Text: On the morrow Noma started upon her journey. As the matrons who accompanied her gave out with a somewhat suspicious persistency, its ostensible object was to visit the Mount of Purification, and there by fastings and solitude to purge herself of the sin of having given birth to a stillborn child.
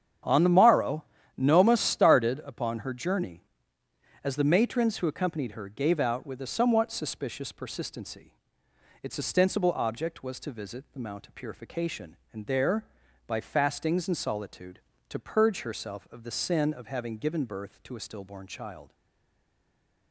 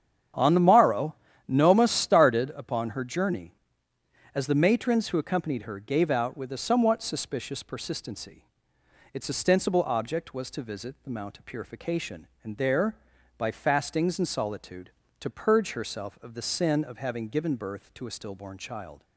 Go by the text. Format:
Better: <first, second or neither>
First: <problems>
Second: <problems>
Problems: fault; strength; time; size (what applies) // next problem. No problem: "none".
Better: second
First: starts louder than the rest; strong; until 1.5 s; 8.5 dB // pauses between "morrow" and "Noma"; slight; at 1.0 s; 0.32 s long // stays silent after the last word; noticeable; from 18.9 s on; 1.2 s long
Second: starts louder than the rest; strong; until 1.6 s; 8.5 dB // pauses between "morrow" and "Noma"; slight; at 1.1 s; 0.32 s long